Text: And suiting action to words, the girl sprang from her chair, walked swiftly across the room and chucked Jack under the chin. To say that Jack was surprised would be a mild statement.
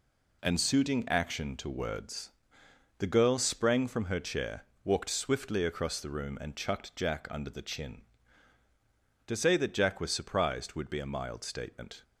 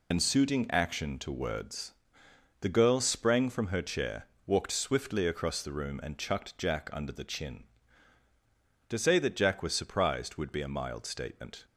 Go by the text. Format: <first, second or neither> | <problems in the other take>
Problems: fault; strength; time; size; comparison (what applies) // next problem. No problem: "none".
first | loses the start of "And"; at 0.1 s; 75 ms